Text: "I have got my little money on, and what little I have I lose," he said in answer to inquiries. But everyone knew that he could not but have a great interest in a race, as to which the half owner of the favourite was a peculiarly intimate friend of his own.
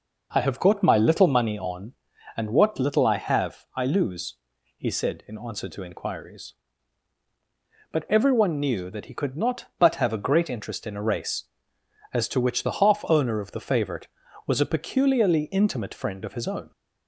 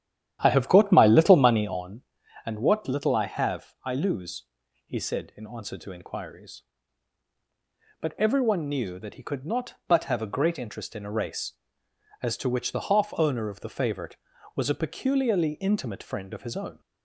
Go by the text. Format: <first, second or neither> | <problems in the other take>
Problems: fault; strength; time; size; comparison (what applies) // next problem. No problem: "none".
first | starts louder than the rest; strong; until 1.8 s; 10.5 dB